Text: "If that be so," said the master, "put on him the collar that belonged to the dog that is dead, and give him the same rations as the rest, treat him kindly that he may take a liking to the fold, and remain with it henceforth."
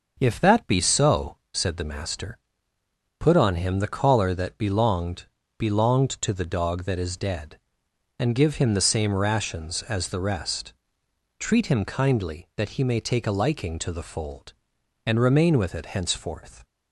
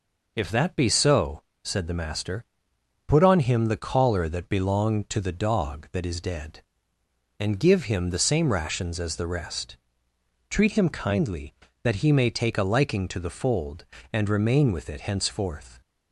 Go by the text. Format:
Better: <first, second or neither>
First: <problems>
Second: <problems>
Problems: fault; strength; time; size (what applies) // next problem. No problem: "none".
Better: second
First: starts louder than the rest; until 1.2 s; 6.5 dB // says "belonged" twice; at 5.5 s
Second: none